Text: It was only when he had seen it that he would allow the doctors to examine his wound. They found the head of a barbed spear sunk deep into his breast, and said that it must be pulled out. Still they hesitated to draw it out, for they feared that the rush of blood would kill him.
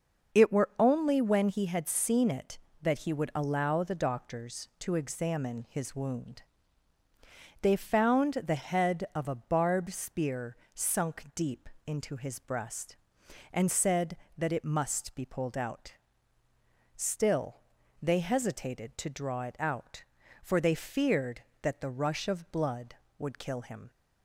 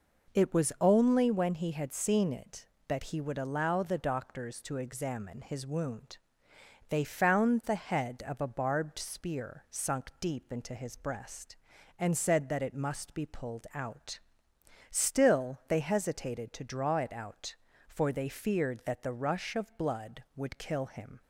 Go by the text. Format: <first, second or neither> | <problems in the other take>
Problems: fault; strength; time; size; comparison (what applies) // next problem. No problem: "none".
second | starts louder than the rest; until 1.4 s; 6 dB // says "were" for "was"; at 0.5 s // pauses between "spear" and "sunk"; slight; at 10.5 s; 0.18 s long // pauses between "deep" and "into"; slight; at 11.6 s; 0.18 s long // pauses between "Still" and "they"; at 17.6 s; 0.40 s long